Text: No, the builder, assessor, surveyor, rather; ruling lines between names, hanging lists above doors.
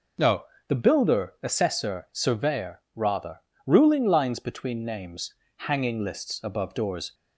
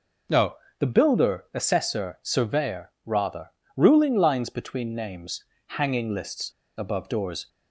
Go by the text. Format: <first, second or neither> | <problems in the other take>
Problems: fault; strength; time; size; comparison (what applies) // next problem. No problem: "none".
first | pauses between "lists" and "above"; slight; at 6.4 s; 0.28 s long